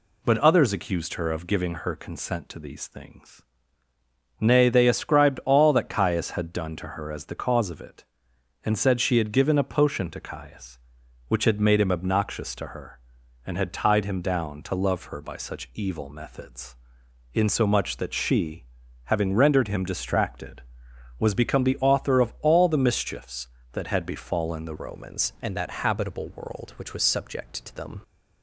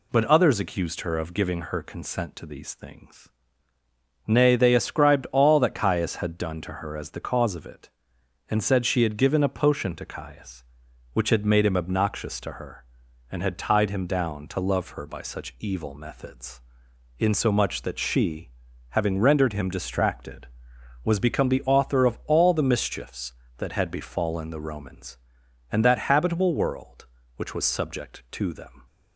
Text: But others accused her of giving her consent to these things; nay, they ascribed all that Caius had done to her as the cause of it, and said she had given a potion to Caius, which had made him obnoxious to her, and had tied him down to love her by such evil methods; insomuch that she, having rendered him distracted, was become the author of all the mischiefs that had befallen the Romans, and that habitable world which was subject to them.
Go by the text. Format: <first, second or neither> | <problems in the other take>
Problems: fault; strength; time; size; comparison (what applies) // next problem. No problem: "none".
second | changes voice at "Romans"; from 24.7 s on; 3.3 s long